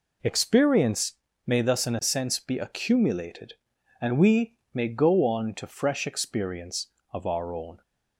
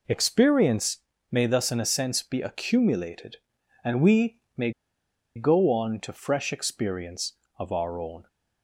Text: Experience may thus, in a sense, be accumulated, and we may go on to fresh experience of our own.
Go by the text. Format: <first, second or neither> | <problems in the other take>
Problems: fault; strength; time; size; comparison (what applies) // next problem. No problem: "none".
first | pauses between "Experience" and "may"; slight; at 0.9 s; 0.32 s long; slight in the first // pauses between "we" and "may"; slight; at 4.3 s; 0.18 s long; slight in the first // pauses between "may" and "go"; noticeable; at 4.7 s; 0.65 s long